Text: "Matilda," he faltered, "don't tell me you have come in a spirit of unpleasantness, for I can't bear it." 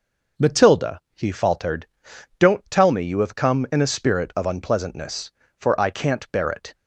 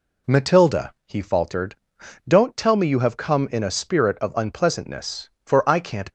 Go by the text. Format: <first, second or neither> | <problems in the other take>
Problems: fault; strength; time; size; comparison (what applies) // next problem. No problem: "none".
first | stops before "bear it"; at 6.0 s